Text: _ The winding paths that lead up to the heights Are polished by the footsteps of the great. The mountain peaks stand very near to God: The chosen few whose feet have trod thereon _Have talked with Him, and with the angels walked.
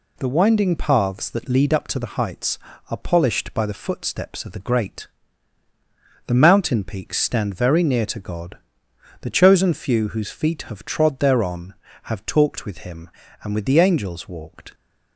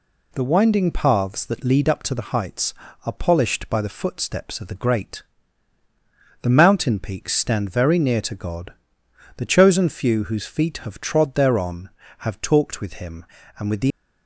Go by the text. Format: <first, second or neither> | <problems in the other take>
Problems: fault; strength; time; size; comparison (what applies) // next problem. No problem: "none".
first | stops before "angels walked"; at 13.9 s